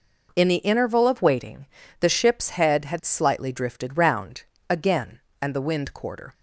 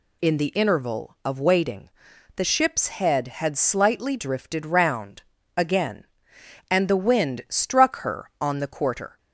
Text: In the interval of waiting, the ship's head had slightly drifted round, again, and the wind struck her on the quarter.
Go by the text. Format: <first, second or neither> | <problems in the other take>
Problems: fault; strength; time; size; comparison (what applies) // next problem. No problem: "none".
second | skips "struck her on the"; at 5.9 s